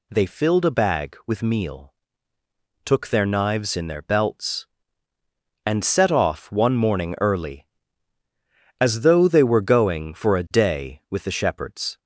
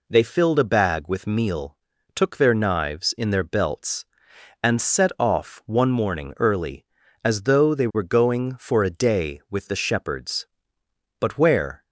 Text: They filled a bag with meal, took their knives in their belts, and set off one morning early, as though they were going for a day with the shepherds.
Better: first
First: none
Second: goes on to say "But where"; noticeable; from 11.1 s on; 0.64 s long

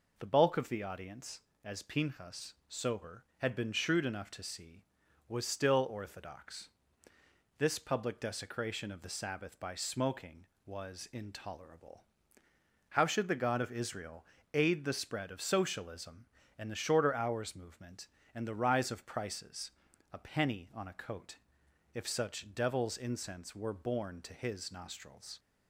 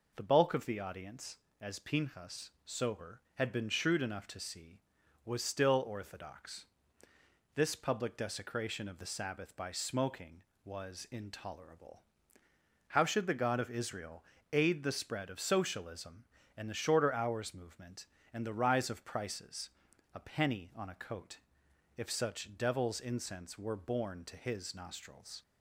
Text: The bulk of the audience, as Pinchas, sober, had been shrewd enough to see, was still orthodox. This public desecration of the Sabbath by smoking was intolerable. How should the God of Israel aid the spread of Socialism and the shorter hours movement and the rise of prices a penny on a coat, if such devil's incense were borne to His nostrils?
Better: neither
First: pauses between "Israel" and "aid"; slight; at 14.2 s; 0.28 s long // pauses between "prices" and "a"; at 19.7 s; 0.40 s long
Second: pauses between "Israel" and "aid"; slight; at 14.2 s; 0.28 s long // pauses between "prices" and "a"; at 19.7 s; 0.42 s long

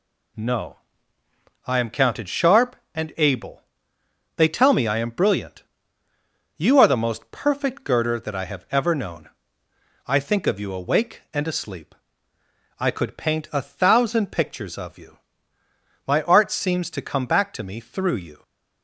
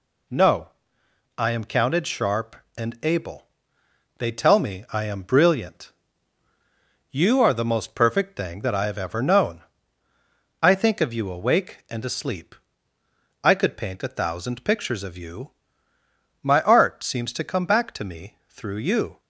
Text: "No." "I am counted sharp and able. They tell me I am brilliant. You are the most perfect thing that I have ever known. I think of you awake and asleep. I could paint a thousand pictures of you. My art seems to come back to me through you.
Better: second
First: says "girder" for "thing"; at 7.8 s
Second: none

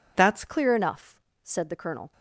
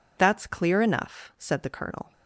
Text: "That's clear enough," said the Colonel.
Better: second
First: changes voice at "clear"; from 0.4 s on; 1.7 s long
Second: none

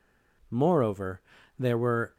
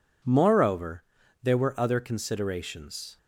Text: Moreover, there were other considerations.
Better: second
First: stops before "other considerations"; at 2.1 s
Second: none

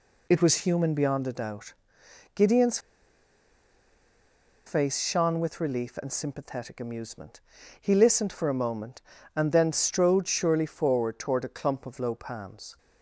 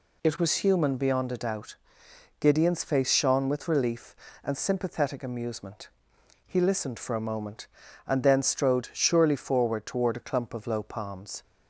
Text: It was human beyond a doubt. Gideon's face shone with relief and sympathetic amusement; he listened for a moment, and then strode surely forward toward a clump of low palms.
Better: second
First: pauses between "Gideon's" and "face"; strong; at 2.7 s; 1.8 s long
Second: none

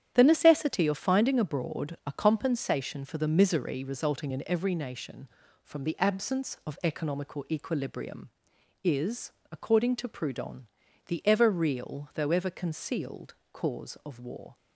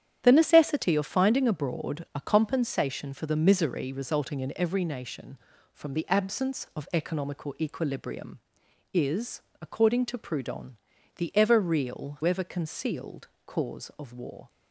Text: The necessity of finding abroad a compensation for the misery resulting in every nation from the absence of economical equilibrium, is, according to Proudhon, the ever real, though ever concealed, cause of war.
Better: first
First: starts louder than the rest; strong; until 1.1 s; 10 dB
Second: starts louder than the rest; strong; until 1.2 s; 10 dB // skips "though"; at 12.2 s

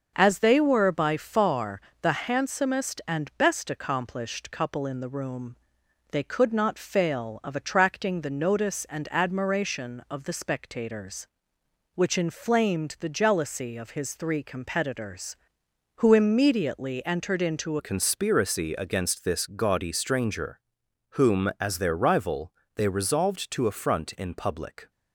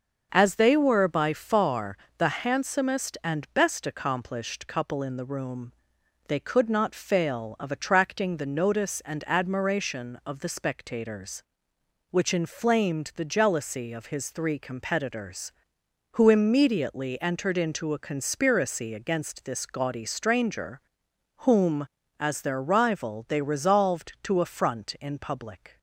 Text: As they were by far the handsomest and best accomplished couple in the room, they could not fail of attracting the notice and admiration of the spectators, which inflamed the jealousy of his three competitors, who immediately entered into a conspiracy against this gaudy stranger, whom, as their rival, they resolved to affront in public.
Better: second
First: starts louder than the rest; until 1.1 s; 6.5 dB // pauses between "far" and "the"; slight; at 1.8 s; 0.22 s long // changes voice at "a"; from 17.7 s on; 7.2 s long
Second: starts louder than the rest; until 1.3 s; 6.5 dB // pauses between "far" and "the"; slight; at 1.9 s; 0.22 s long

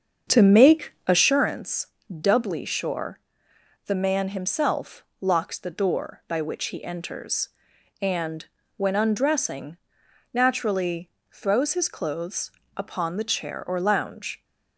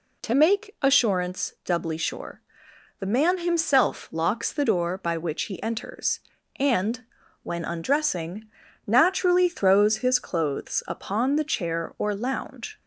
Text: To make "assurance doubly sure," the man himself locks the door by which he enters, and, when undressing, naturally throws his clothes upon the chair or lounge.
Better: second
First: starts louder than the rest; strong; until 1.5 s; 7 dB // pauses between "assurance" and "doubly"; slight; at 1.8 s; 0.28 s long // pauses between "himself" and "locks"; slight; at 5.0 s; 0.20 s long // pauses between "naturally" and "throws"; slight; at 11.0 s; 0.24 s long // pauses between "clothes" and "upon"; slight; at 12.5 s; 0.24 s long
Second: none

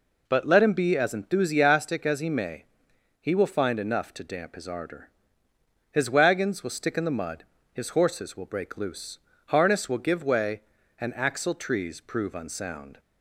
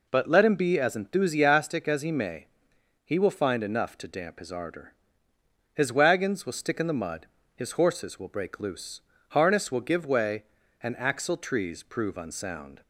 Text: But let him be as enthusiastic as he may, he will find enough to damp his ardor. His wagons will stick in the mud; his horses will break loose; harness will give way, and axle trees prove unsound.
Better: neither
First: none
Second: none

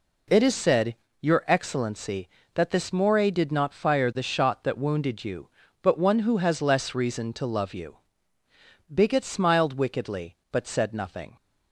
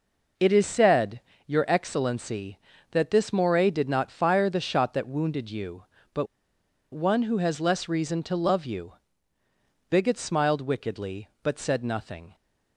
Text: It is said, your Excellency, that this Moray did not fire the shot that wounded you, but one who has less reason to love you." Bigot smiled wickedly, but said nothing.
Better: first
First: none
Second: pauses between "but" and "one"; noticeable; at 6.2 s; 0.66 s long

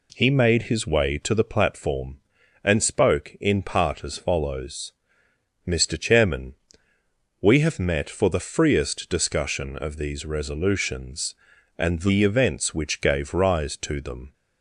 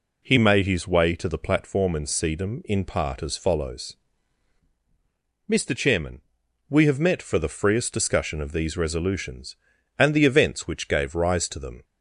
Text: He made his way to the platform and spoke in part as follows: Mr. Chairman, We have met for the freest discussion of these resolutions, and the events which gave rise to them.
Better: first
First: none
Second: says "sedum" for "spoke"; at 2.0 s

